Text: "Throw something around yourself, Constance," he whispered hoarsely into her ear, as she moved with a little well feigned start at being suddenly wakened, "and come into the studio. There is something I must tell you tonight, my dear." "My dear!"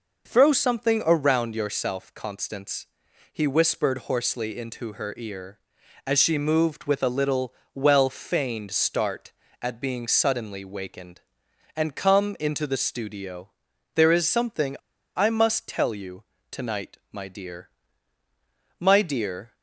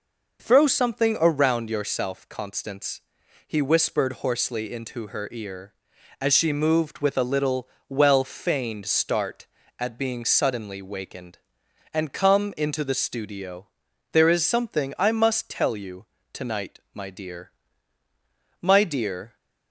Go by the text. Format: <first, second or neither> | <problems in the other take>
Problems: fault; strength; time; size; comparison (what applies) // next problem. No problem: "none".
second | pauses between "little" and "well"; slight; at 7.5 s; 0.20 s long; slight in the second // pauses between "something" and "I"; at 14.7 s; 0.39 s long // pauses between "you" and "tonight"; slight; at 16.2 s; 0.30 s long; slight in the second